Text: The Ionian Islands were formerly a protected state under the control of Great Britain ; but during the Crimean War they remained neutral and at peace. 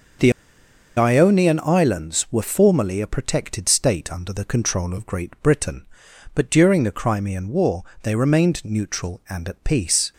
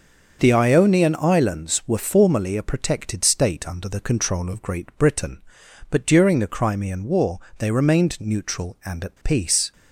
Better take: second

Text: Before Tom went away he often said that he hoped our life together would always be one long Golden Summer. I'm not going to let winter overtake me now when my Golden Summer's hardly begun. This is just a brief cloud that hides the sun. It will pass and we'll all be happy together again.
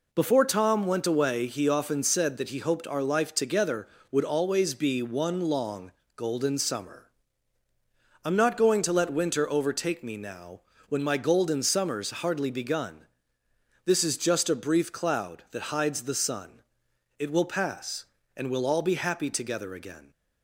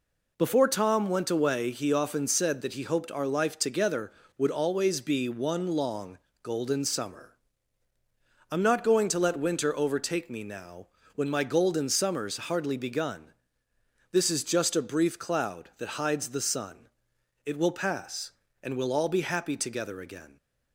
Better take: neither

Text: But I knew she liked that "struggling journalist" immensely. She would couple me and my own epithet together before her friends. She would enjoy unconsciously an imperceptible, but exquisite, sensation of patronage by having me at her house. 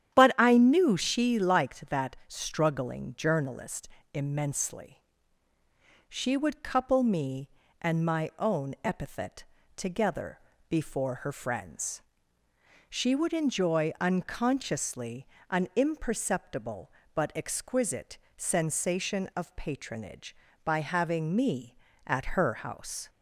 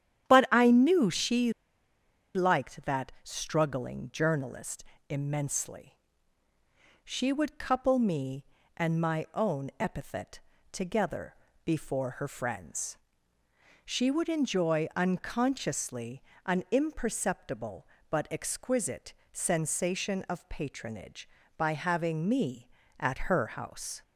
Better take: first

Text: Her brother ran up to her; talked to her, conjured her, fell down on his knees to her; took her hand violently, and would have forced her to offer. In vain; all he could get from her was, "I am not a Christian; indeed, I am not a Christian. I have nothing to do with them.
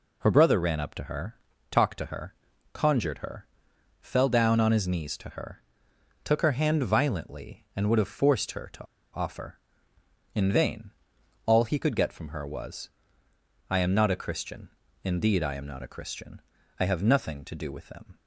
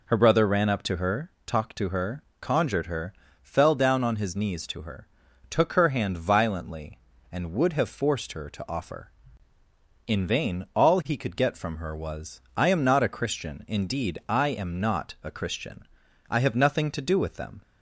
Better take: second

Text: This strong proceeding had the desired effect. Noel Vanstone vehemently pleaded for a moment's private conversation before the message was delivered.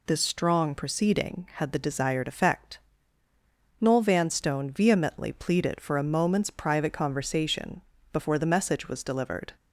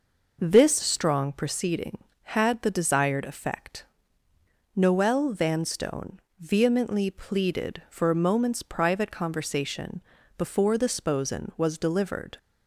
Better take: first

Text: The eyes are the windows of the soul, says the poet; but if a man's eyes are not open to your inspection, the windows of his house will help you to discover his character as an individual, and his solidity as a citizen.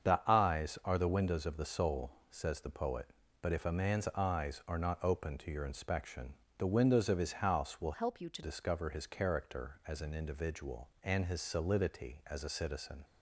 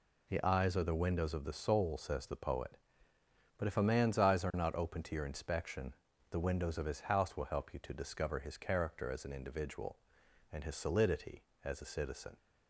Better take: second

